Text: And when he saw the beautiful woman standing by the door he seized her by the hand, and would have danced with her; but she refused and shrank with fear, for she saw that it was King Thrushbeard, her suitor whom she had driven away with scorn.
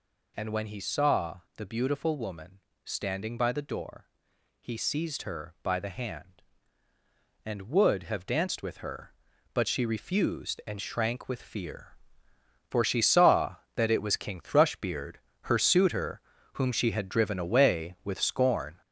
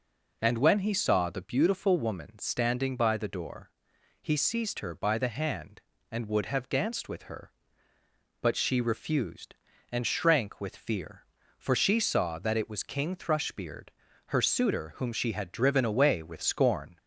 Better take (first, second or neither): second